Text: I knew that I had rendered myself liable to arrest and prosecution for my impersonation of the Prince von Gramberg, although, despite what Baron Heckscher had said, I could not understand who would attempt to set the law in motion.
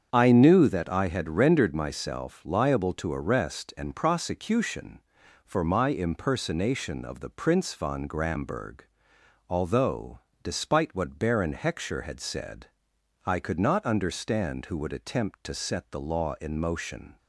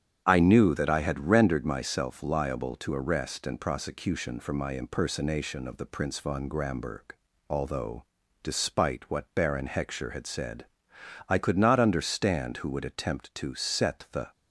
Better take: first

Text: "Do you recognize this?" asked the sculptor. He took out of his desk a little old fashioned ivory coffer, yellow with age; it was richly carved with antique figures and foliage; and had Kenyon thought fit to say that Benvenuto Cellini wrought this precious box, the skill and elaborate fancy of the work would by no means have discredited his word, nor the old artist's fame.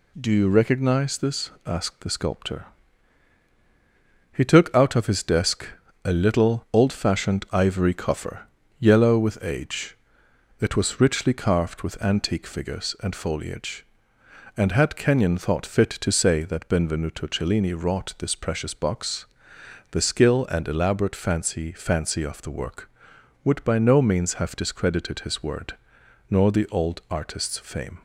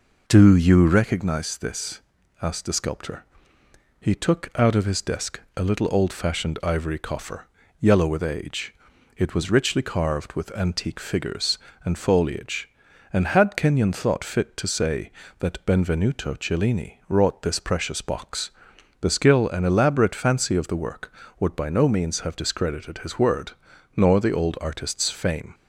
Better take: second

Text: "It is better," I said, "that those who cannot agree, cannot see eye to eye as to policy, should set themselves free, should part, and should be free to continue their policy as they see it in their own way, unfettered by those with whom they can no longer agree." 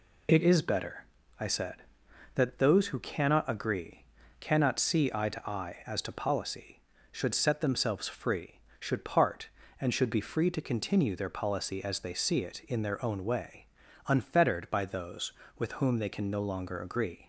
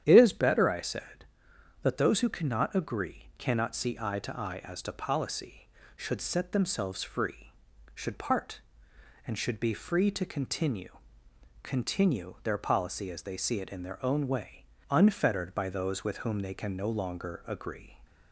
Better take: first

